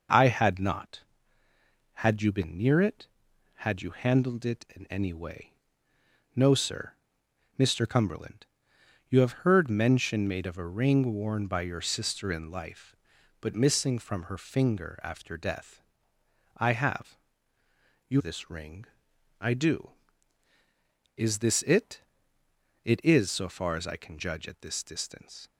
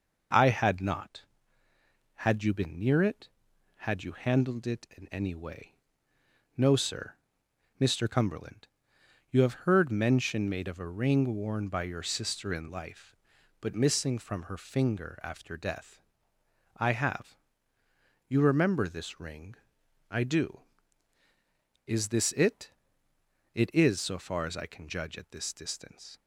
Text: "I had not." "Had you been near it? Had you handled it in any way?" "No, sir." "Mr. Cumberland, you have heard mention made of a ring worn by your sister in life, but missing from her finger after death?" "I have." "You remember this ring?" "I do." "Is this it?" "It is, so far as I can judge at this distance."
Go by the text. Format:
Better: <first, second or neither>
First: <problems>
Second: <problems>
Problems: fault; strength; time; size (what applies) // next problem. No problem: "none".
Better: second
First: skips "remember"; at 18.1 s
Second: none